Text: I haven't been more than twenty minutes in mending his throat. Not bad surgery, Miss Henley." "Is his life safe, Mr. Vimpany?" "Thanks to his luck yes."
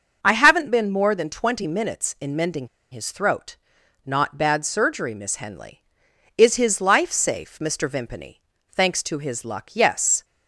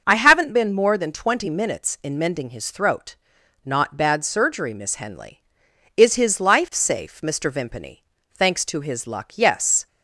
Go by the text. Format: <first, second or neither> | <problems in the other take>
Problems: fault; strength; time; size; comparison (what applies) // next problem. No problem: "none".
second | starts louder than the rest; until 1.2 s; 6 dB; also in the second // pauses between "mending" and "his"; slight; at 2.6 s; 0.24 s long